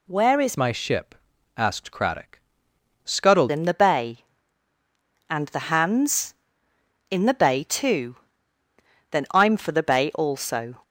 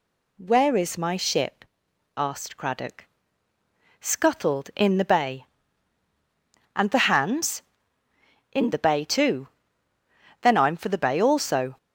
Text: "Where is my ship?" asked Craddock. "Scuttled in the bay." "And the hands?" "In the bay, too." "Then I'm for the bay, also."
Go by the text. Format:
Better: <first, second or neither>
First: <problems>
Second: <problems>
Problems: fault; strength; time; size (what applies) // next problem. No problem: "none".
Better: second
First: changes voice from "my" to "Scuttled"; from 0.5 to 3.5 s; 3.0 s long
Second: none